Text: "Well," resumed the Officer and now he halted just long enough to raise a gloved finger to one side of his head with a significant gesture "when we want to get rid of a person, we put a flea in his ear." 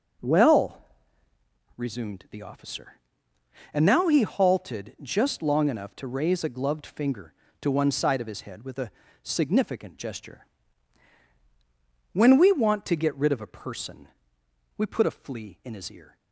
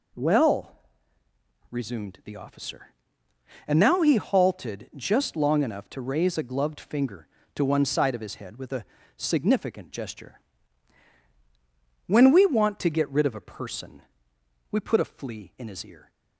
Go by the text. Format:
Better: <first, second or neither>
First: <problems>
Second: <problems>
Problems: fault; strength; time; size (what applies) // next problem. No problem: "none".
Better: second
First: starts louder than the rest; until 1.6 s; 6.5 dB // pauses between "a" and "significant"; slight; at 8.8 s; 0.32 s long // pauses between "gesture" and "when"; strong; at 10.4 s; 1.6 s long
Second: pauses between "a" and "significant"; slight; at 8.8 s; 0.32 s long // pauses between "gesture" and "when"; strong; at 10.3 s; 1.6 s long